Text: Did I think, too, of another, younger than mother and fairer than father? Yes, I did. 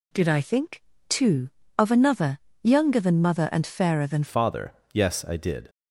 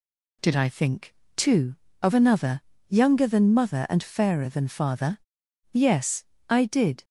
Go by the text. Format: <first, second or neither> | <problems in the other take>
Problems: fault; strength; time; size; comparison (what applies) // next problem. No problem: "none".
second | changes voice at "father"; from 4.2 s on; 1.4 s long